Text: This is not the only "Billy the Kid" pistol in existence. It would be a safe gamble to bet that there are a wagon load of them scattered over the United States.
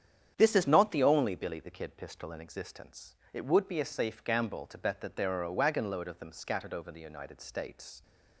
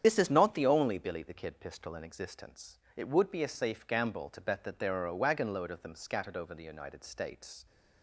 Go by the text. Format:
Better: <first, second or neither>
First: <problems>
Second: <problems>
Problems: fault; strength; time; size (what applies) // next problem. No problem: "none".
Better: first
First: starts louder than the rest; strong; until 1.3 s; 8.5 dB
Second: loses the start of "This"; at 0.0 s; 55 ms // starts louder than the rest; strong; until 1.0 s; 9 dB